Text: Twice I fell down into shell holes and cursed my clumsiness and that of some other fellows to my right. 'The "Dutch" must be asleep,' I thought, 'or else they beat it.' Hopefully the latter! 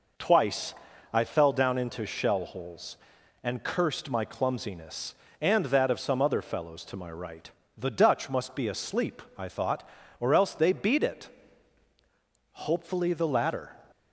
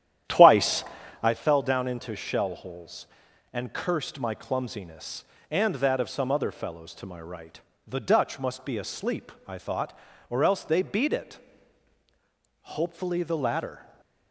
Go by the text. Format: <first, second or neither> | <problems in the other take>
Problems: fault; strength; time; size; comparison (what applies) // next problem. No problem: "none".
first | starts louder than the rest; strong; until 1.4 s; 11 dB // pauses between "Twice" and "I"; at 0.8 s; 0.38 s long; also in the first